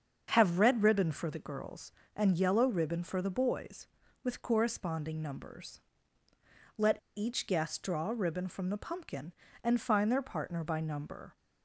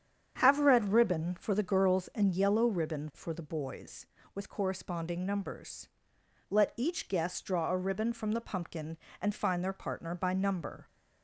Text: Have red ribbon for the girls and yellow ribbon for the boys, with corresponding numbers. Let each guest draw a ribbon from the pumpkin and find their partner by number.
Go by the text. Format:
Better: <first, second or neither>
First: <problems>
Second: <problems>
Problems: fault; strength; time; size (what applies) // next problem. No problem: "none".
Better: second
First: starts louder than the rest; until 1.3 s; 7 dB // pauses between "Let" and "each"; slight; at 6.9 s; 0.18 s long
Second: starts louder than the rest; strong; until 1.4 s; 8 dB